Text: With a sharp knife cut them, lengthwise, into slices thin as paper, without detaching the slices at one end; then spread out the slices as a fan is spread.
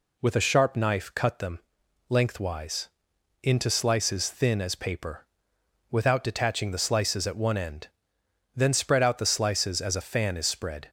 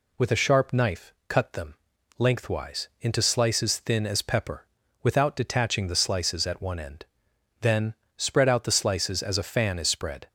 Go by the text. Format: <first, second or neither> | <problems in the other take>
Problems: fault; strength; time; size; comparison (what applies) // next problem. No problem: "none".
first | pauses between "knife" and "cut"; slight; at 1.1 s; 0.16 s long // says "pepper" for "paper"; at 4.2 s // pauses between "then" and "spread"; slight; at 7.9 s; 0.20 s long